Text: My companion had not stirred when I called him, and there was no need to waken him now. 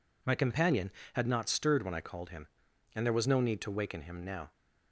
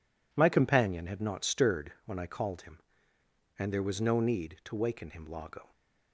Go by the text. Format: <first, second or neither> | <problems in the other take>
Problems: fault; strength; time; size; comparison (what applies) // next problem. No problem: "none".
first | says "lago" for "now"; at 5.2 s